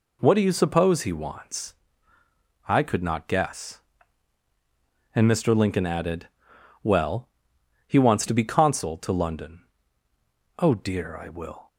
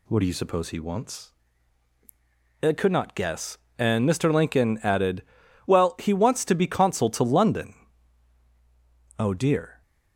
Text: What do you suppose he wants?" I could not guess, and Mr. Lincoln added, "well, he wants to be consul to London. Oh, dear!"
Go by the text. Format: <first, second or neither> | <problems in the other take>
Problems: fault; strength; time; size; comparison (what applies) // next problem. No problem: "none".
second | goes on to say "I will"; from 11.1 s on; 0.52 s long